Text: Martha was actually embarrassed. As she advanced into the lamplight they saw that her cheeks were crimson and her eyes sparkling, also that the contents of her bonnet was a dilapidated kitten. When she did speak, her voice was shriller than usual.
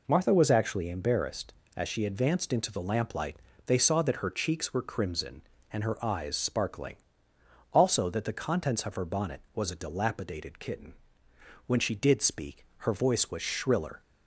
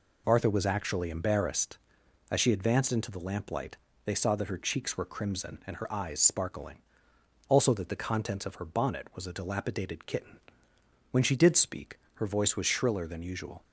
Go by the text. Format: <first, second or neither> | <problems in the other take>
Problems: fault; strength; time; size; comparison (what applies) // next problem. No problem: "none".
second | pauses between "lamplight" and "they"; slight; at 3.3 s; 0.30 s long; slight in the second // stops before "than usual"; at 14.0 s